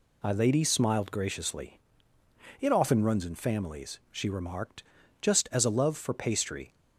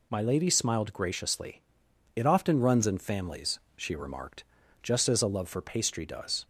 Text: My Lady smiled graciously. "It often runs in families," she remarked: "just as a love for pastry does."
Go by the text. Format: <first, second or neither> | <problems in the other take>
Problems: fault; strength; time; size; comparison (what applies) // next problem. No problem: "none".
second | stops before "does"; at 6.7 s